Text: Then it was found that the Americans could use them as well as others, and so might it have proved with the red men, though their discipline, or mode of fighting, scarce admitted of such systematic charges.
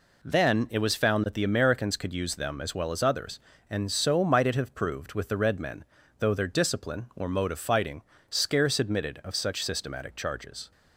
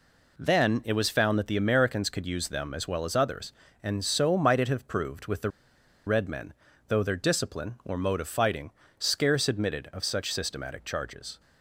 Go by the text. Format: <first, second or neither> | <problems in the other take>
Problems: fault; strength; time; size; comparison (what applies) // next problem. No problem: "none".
first | pauses between "the" and "red"; noticeable; at 5.4 s; 0.56 s long